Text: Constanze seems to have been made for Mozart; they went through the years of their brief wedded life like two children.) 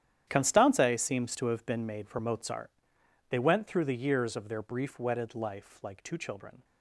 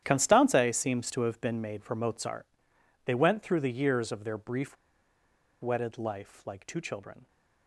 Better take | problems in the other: first | starts louder than the rest; strong; until 1.0 s; 10.5 dB; strong in the first // pauses between "brief" and "wedded"; noticeable; at 4.7 s; 0.85 s long

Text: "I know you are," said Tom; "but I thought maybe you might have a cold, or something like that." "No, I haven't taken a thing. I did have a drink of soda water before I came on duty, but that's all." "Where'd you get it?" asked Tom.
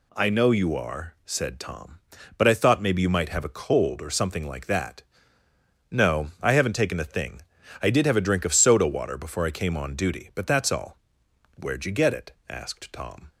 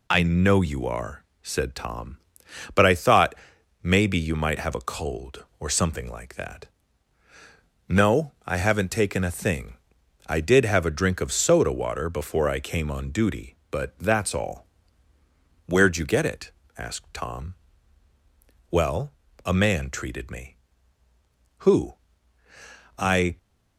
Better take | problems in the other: first | pauses between "thought" and "maybe"; noticeable; at 3.3 s; 0.48 s long // goes on to say "Well a man treated me Who I"; strong; from 18.6 s on; 4.6 s long

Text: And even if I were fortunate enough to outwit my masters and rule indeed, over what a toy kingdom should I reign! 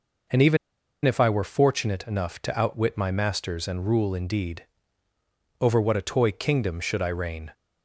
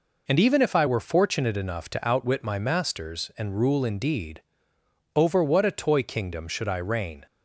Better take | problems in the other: second | pauses between "even" and "if"; noticeable; at 0.5 s; 0.47 s long

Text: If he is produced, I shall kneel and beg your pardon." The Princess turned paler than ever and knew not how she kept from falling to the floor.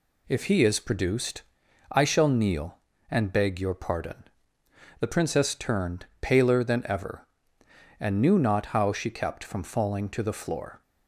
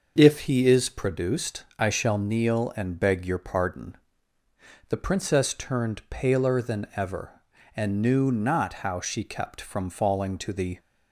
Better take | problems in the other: first | starts louder than the rest; until 1.1 s; 6 dB // stops before "floor"; at 10.7 s

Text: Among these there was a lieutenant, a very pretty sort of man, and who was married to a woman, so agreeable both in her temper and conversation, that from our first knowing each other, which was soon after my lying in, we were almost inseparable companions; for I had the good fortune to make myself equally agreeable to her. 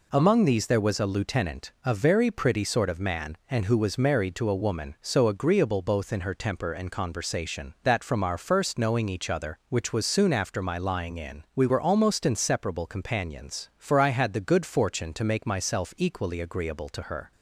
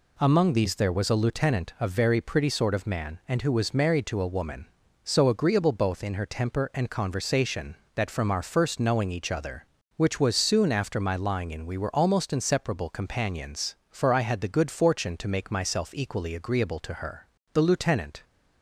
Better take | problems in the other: first | goes on to say "The lieutenant"; noticeable; from 17.5 s on; 0.70 s long

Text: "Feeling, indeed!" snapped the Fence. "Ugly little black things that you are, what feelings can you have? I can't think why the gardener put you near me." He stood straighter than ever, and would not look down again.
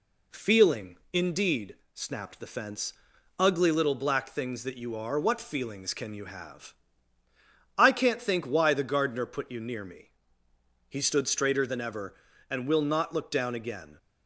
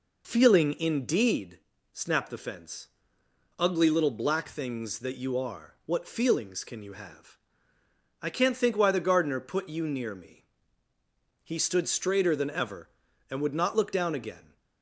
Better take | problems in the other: second | says "will" for "would"; at 12.6 s

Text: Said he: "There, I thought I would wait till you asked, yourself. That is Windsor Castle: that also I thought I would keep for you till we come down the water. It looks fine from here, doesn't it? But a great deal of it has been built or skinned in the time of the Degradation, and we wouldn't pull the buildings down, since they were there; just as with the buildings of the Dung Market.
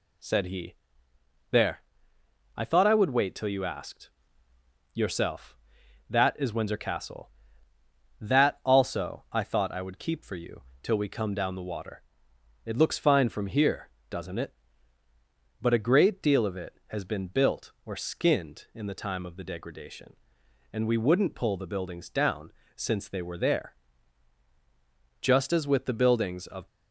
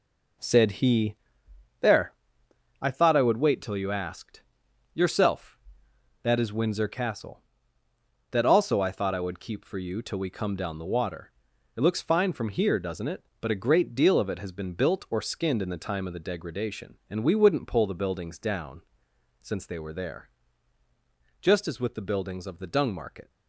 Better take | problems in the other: second | pauses between "you" and "till"; slight; at 10.6 s; 0.20 s long // stops before "the Dung Market"; at 26.6 s

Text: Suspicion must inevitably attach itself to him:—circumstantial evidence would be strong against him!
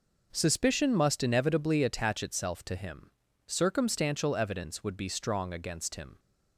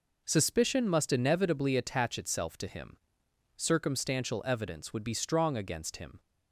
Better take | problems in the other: neither | none

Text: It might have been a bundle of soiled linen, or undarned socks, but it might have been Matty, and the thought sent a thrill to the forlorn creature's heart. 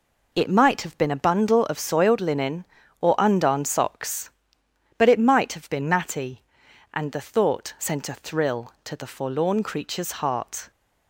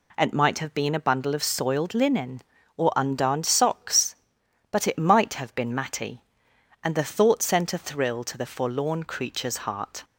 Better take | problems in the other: neither | none

